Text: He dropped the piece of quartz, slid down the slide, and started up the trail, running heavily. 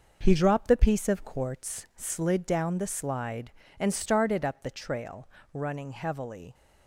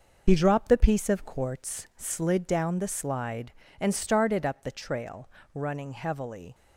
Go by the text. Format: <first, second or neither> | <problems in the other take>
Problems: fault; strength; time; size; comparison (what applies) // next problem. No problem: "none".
first | loses the start of "He"; at 0.2 s; 60 ms